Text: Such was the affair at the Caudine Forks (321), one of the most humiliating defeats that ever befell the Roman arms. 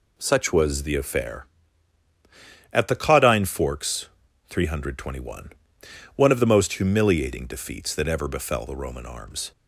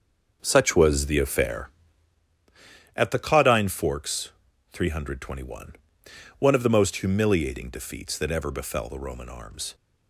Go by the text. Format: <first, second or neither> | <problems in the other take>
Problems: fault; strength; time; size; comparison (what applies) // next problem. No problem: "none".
first | starts louder than the rest; until 2.3 s; 6.5 dB